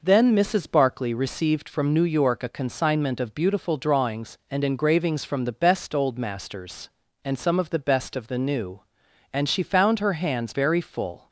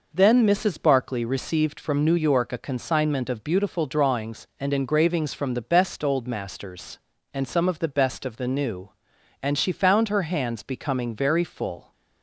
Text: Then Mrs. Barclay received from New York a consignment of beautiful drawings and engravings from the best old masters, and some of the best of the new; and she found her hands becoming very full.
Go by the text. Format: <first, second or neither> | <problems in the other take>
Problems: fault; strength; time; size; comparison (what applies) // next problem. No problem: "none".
second | skips "becoming"; at 10.5 s